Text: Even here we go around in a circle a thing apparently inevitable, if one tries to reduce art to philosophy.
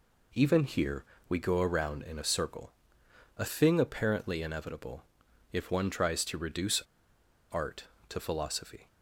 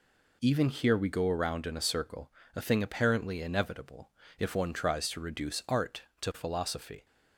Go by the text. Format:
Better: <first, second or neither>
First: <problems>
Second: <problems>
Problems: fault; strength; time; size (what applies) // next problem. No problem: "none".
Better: second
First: pauses between "here" and "we"; slight; at 1.0 s; 0.24 s long // pauses between "circle" and "a"; noticeable; at 2.7 s; 0.68 s long // pauses between "reduce" and "art"; noticeable; at 6.8 s; 0.68 s long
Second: pauses between "circle" and "a"; slight; at 2.3 s; 0.24 s long